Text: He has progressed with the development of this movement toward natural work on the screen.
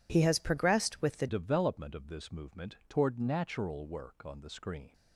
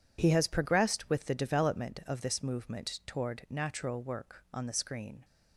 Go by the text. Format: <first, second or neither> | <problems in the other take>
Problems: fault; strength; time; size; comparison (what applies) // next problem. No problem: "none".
second | changes voice at "development"; from 1.2 s on; 3.7 s long